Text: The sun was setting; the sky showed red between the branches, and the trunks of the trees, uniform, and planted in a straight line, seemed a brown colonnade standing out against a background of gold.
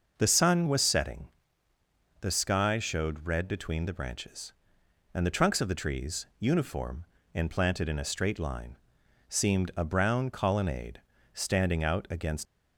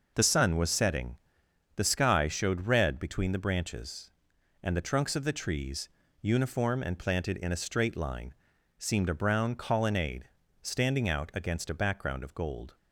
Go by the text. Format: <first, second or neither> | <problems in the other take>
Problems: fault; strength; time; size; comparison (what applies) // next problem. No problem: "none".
second | pauses between "colonnade" and "standing"; slight; at 11.0 s; 0.32 s long; slight in the second // stops before "a background of gold"; at 12.4 s